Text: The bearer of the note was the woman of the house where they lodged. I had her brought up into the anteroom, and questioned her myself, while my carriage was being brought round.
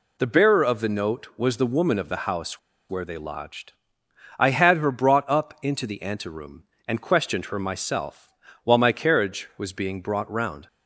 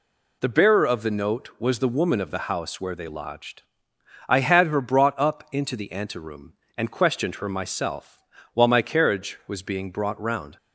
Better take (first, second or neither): second